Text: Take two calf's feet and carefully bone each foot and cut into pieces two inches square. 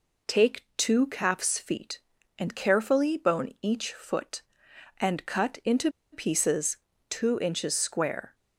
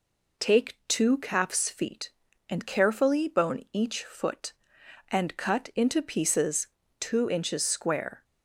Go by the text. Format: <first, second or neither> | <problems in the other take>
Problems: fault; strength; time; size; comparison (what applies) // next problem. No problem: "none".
second | pauses between "into" and "pieces"; slight; at 5.9 s; 0.22 s long // pauses between "pieces" and "two"; slight; at 6.7 s; 0.32 s long; slight in the second